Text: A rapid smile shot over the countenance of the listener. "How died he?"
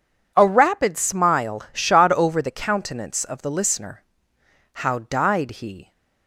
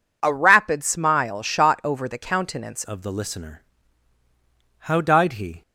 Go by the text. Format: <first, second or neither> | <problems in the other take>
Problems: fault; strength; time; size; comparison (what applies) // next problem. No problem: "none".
first | changes voice at "of"; from 2.8 s on; 2.8 s long